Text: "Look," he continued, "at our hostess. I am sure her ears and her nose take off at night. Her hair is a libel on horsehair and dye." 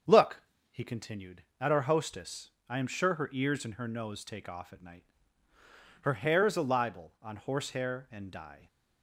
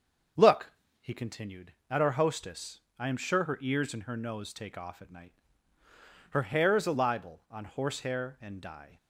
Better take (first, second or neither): neither